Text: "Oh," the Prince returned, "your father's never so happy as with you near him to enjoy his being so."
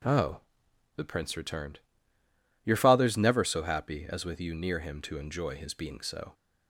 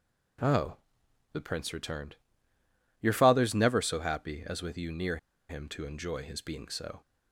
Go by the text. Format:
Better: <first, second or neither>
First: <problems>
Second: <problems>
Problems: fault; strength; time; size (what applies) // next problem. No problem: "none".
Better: first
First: none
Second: pauses between "near" and "him"; slight; at 5.1 s; 0.31 s long